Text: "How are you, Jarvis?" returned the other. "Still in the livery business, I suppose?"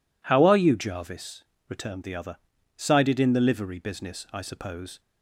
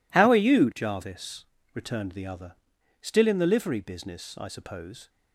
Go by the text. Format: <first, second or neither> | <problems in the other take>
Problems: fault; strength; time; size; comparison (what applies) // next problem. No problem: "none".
second | says "Sided" for "Still"; at 2.7 s